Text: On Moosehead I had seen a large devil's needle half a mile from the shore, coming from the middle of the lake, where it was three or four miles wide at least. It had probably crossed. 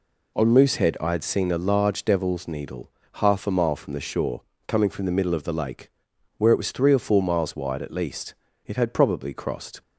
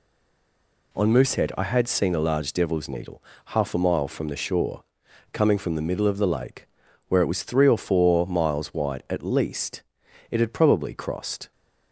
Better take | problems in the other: first | stays silent before the first word; slight; until 0.9 s; 0.9 s long // pauses between "needle" and "half"; slight; at 3.2 s; 0.22 s long; slight in the first

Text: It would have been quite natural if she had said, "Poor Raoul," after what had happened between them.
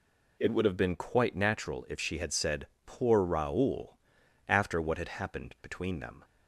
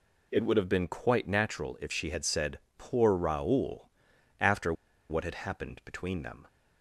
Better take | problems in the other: first | pauses between "after" and "what"; at 4.7 s; 0.37 s long

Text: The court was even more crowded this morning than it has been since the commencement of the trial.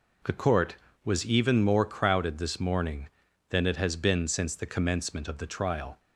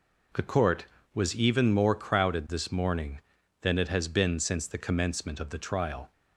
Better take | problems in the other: neither | none

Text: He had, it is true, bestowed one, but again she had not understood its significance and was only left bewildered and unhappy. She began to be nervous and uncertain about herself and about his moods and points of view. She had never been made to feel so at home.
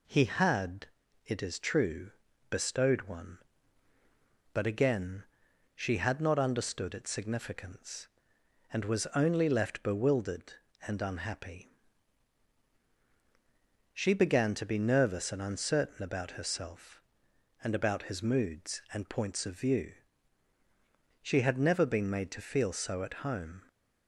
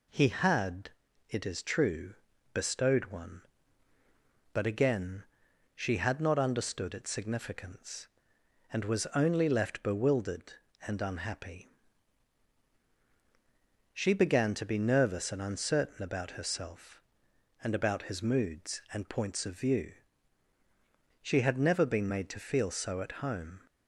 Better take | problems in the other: neither | pauses between "again" and "she"; noticeable; the same in both

